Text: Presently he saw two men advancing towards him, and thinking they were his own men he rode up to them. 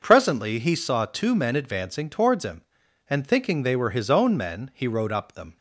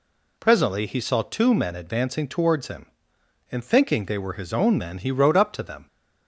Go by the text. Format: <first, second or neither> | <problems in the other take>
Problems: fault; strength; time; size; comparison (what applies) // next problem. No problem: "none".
second | starts louder than the rest; noticeable; until 1.0 s; 6 dB // skips "to"; at 5.3 s